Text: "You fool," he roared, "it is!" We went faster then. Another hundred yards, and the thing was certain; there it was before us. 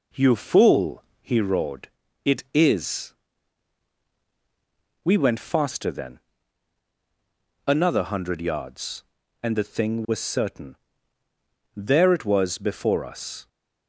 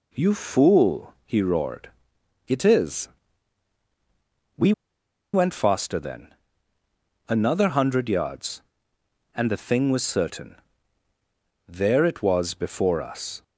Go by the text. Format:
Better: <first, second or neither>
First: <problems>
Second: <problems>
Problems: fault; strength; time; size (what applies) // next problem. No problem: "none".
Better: first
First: none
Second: pauses between "We" and "went"; noticeable; at 4.7 s; 0.60 s long